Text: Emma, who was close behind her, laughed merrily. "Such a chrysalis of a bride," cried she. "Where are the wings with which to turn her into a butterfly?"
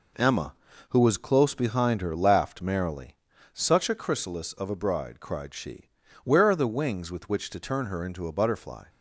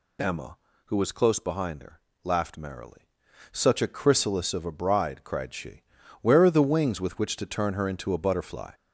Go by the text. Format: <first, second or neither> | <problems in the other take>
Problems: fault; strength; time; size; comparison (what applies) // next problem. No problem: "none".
first | gets louder; noticeable; throughout; 5 dB